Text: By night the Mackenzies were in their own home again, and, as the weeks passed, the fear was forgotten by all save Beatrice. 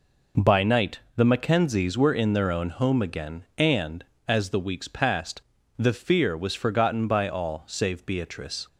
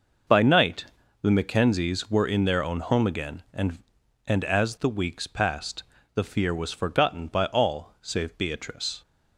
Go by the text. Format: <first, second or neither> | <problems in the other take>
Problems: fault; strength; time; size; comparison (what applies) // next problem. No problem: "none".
first | starts louder than the rest; noticeable; until 1.6 s; 6 dB // pauses between "night" and "the"; at 0.8 s; 0.38 s long; slight in the first // says "and" twice; at 4.2 s